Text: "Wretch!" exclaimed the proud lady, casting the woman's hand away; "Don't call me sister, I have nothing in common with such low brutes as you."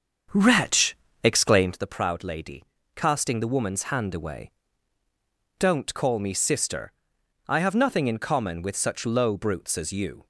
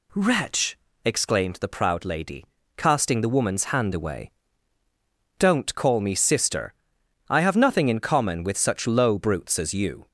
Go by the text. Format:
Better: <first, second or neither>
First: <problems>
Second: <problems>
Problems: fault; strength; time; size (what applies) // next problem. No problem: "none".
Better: second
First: starts louder than the rest; strong; until 1.9 s; 7.5 dB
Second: none